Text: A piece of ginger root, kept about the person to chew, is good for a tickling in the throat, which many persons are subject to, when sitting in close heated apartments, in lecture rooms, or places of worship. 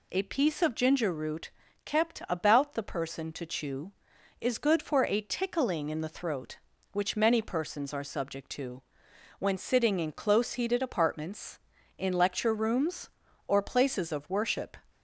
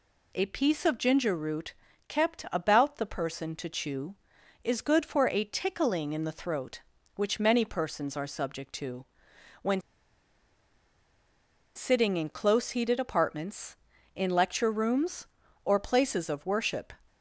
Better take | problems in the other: first | pauses between "when" and "sitting"; strong; at 9.7 s; 1.9 s long

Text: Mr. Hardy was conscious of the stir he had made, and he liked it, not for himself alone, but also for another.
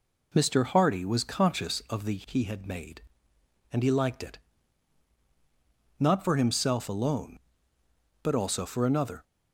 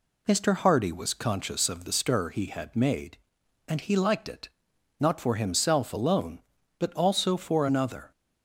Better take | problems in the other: second | skips "stir"; at 2.2 s

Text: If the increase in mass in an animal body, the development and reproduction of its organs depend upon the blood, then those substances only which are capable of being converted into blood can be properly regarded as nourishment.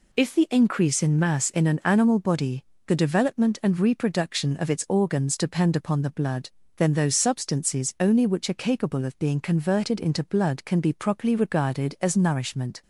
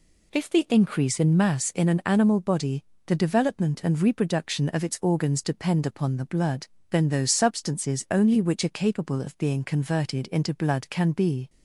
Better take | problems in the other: first | stops before "properly regarded as nourishment"; at 11.4 s

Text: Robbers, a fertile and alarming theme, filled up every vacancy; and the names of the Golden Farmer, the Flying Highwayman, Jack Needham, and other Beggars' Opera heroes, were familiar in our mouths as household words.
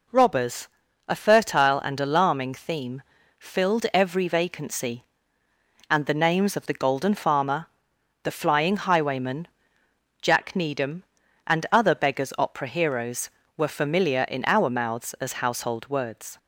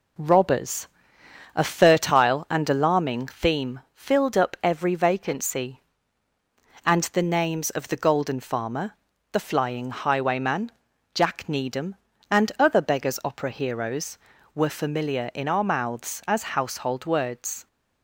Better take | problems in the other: second | skips "up"; at 3.8 s

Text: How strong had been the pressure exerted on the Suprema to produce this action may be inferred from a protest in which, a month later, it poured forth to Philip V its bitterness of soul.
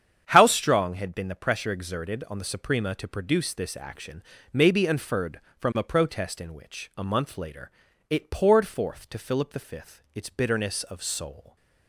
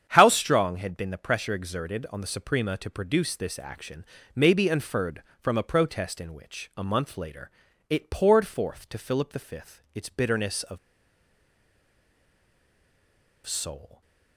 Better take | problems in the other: first | starts louder than the rest; strong; until 1.1 s; 8.5 dB; strong in the first // pauses between "action" and "may"; slight; at 4.0 s; 0.30 s long; slight in the first // pauses between "of" and "soul"; strong; at 10.7 s; 2.6 s long

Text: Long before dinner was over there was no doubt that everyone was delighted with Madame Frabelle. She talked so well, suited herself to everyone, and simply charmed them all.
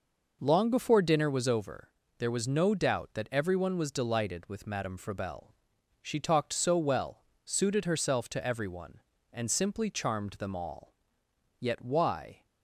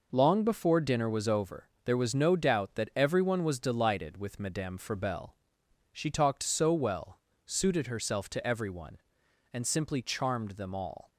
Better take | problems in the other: second | pauses between "over" and "there"; slight; at 1.8 s; 0.30 s long; slight in the second // goes on to say "Yet why"; noticeable; from 11.5 s on; 0.86 s long

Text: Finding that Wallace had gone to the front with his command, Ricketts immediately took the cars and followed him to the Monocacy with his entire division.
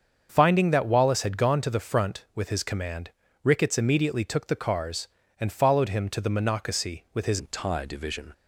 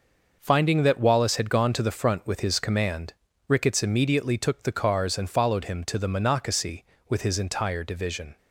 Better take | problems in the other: second | starts louder than the rest; until 1.3 s; 7 dB // changes voice at "entire"; from 7.3 s on; 1.0 s long

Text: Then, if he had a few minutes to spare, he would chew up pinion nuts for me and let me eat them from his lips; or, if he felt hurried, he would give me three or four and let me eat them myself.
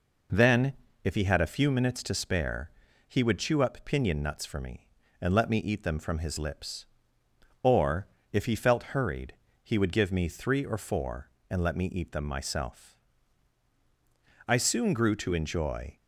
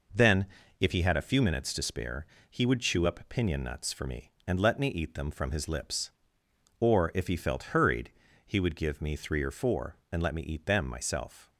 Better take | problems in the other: second | goes on to say "I soon grew to enjoy"; from 14.4 s on; 1.5 s long

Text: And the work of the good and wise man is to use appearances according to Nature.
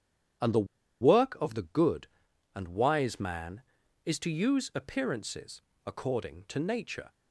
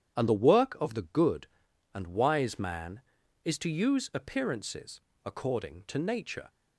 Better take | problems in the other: second | starts louder than the rest; strong; until 1.8 s; 9.5 dB; strong in the second // pauses between "the" and "work"; at 0.6 s; 0.37 s long // pauses between "appearances" and "according"; slight; at 5.6 s; 0.22 s long; slight in the second

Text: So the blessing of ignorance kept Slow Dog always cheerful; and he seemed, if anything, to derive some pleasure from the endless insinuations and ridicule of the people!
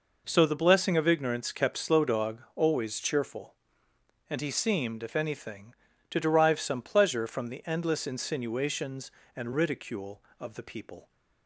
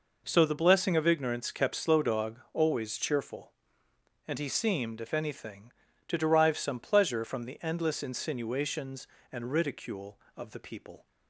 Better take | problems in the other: neither | none

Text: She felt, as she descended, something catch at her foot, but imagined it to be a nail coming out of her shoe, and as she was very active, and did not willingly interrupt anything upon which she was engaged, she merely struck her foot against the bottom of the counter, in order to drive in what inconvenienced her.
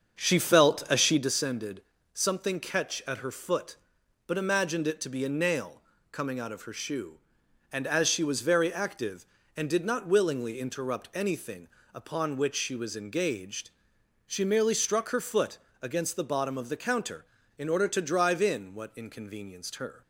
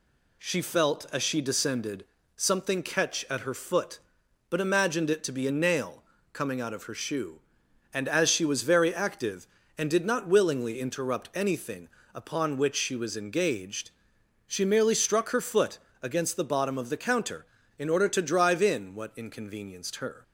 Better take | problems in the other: second | starts louder than the rest; until 1.3 s; 7 dB // pauses between "nail" and "coming"; slight; at 5.8 s; 0.28 s long; slight in the second // pauses between "anything" and "upon"; slight; at 11.6 s; 0.24 s long; slight in the second // pauses between "foot" and "against"; slight; at 15.5 s; 0.24 s long; slight in the second

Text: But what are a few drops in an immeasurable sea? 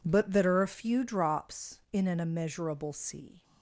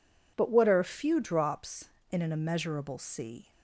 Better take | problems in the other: second | says "that" for "what"; at 0.3 s

